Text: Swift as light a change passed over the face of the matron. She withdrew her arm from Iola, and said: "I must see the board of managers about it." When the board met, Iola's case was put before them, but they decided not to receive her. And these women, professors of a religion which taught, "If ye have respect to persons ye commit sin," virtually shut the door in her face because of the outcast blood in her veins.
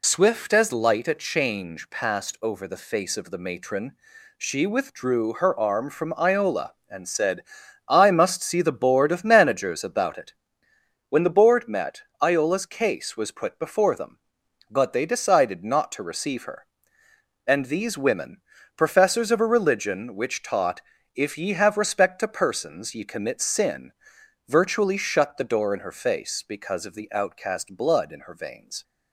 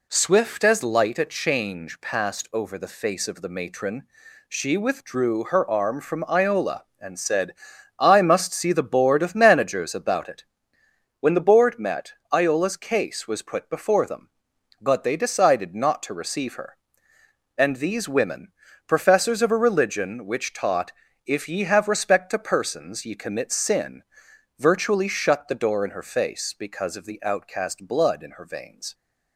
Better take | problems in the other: second | loses the start of "Swift"; at 0.0 s; 45 ms

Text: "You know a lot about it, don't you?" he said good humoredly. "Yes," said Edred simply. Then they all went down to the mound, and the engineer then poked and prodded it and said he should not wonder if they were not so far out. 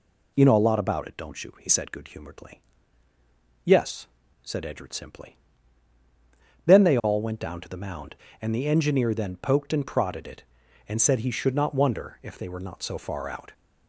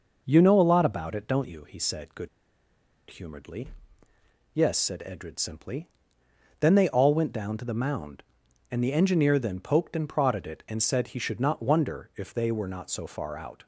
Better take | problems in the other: first | pauses between "good" and "humoredly"; noticeable; at 2.2 s; 0.82 s long

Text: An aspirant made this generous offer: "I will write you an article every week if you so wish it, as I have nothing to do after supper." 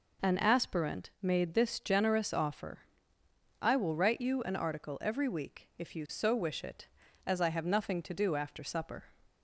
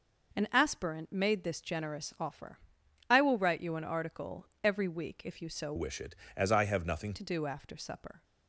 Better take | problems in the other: first | pauses between "article" and "every"; slight; at 4.4 s; 0.18 s long // changes voice from "wish" to "nothing"; from 5.7 to 7.1 s; 1.4 s long

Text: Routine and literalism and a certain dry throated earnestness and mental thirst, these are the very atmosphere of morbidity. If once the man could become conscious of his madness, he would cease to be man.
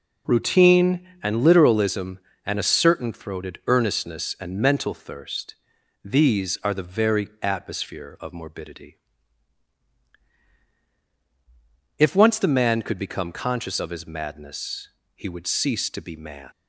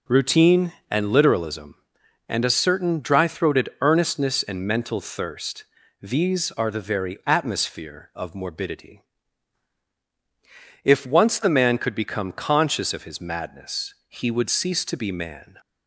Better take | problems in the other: second | skips "dry"; at 3.1 s

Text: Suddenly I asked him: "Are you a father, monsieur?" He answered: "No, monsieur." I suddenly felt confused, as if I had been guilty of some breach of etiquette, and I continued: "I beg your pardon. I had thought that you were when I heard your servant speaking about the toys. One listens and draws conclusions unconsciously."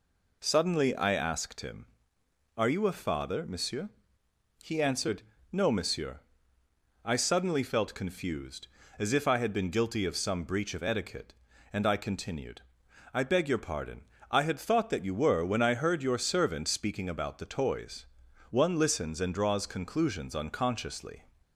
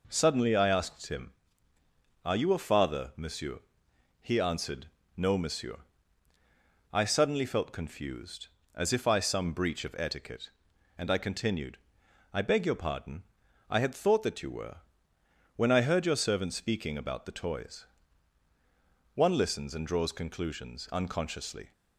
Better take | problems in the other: first | skips "had been guilty of"; at 9.1 s // pauses between "were" and "when"; noticeable; at 14.7 s; 0.78 s long

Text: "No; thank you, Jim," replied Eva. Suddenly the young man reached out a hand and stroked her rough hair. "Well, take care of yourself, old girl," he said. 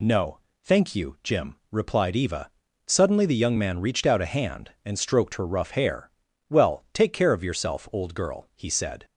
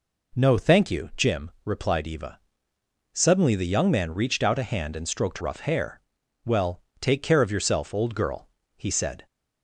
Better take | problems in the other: first | skips "her"; at 5.3 s

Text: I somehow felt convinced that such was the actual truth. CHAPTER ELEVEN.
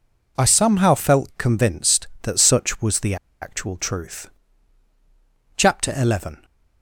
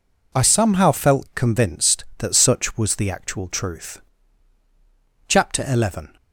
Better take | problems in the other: second | pauses between "the" and "actual"; slight; at 3.1 s; 0.26 s long

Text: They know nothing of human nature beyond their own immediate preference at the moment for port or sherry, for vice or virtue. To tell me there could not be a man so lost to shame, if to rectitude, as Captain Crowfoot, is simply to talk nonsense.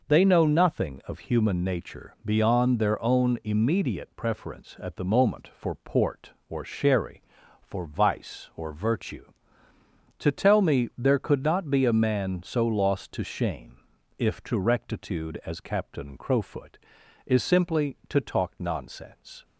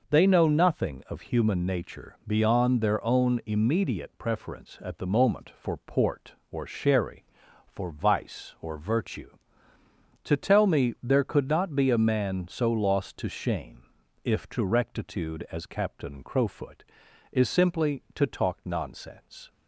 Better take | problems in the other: neither | none

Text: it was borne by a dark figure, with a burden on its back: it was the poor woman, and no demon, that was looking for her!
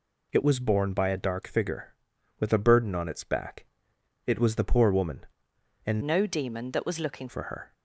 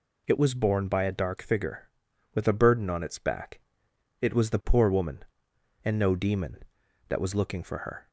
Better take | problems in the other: second | changes voice from "no" to "looking"; from 6.0 to 7.2 s; 1.2 s long

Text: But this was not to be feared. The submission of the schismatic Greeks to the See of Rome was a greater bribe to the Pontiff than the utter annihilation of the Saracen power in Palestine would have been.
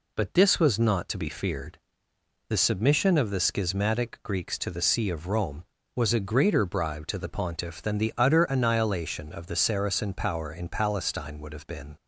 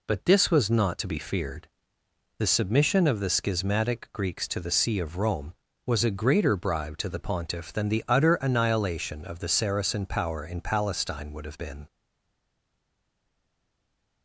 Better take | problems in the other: first | stays silent after the last word; from 11.8 s on; 2.4 s long

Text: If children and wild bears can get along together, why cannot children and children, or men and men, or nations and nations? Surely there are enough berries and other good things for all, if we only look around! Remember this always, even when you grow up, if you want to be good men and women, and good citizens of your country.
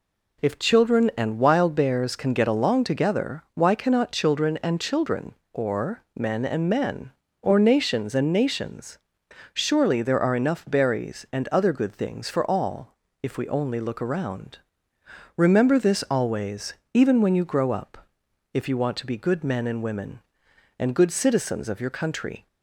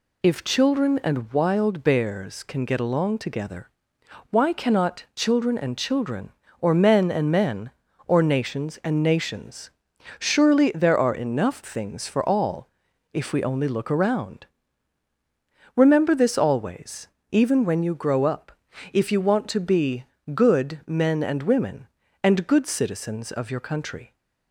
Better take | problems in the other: first | skips "berries and other good"; at 11.6 s // pauses between "be" and "good"; slight; at 20.0 s; 0.28 s long

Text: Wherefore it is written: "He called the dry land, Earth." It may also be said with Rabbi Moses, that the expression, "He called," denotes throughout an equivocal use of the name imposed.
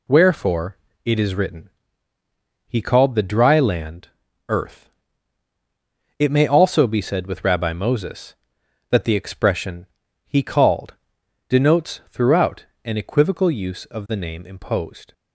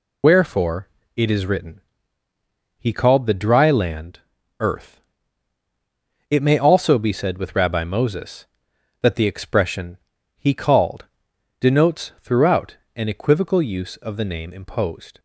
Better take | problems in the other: first | loses the start of "Wherefore"; at 0.2 s; 50 ms // pauses between "Wherefore" and "it"; slight; at 0.8 s; 0.26 s long; slight in the first // pauses between "throughout" and "an"; slight; at 12.7 s; 0.22 s long; slight in the first

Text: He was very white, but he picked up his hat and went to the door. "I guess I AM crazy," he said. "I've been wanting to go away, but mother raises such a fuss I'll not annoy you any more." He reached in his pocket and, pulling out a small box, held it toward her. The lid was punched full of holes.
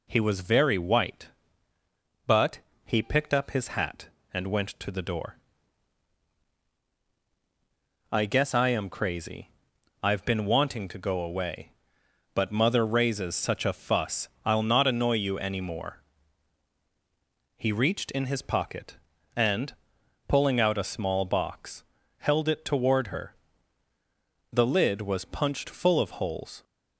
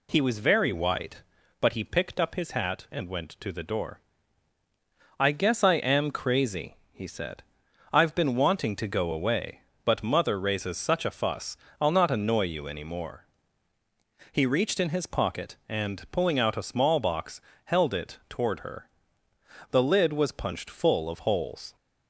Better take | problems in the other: second | pauses between "but" and "he"; slight; at 2.6 s; 0.22 s long // skips "he said"; at 9.7 s // pauses between "fuss" and "I'll"; slight; at 14.2 s; 0.16 s long; slight in the second

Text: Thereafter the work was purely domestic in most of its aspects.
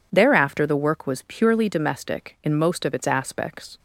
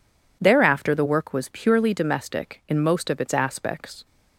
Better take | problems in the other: neither | none

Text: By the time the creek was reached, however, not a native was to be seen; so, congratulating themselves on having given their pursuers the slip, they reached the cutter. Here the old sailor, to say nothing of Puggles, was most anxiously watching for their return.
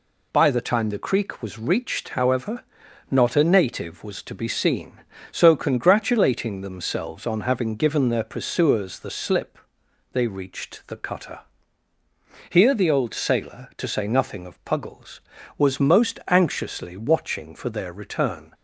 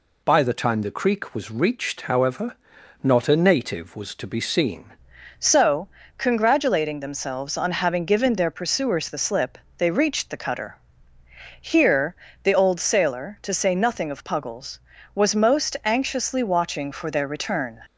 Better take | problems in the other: first | changes voice at "so"; from 5.3 s on; 12.4 s long // pauses between "Here" and "the"; slight; at 12.1 s; 0.30 s long

